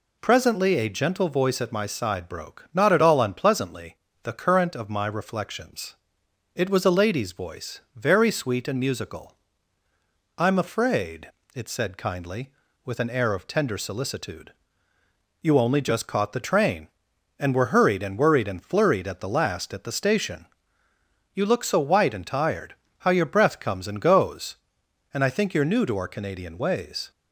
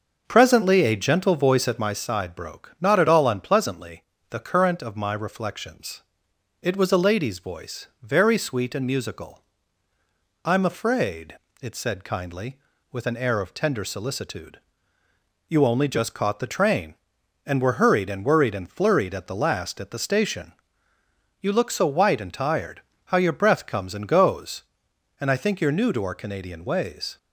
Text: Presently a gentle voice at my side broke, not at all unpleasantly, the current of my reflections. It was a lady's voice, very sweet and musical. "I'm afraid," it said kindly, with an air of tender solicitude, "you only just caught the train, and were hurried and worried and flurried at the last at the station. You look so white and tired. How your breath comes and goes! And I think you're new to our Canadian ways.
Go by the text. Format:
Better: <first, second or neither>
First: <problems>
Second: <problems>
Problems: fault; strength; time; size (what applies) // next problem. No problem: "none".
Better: first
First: none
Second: starts louder than the rest; until 2.1 s; 6.5 dB